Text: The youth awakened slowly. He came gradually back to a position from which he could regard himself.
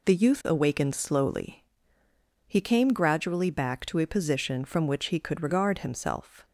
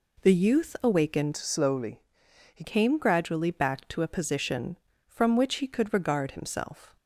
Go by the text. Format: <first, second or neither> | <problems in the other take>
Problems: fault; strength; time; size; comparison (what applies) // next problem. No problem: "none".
first | changes voice from "slowly" to "He"; from 1.3 to 2.6 s; 1.3 s long